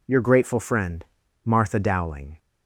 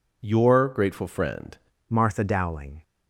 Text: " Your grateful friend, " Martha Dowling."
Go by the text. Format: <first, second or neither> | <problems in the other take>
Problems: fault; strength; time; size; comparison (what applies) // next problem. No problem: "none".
first | changes voice from "Your" to "friend"; from 0.2 to 1.5 s; 1.3 s long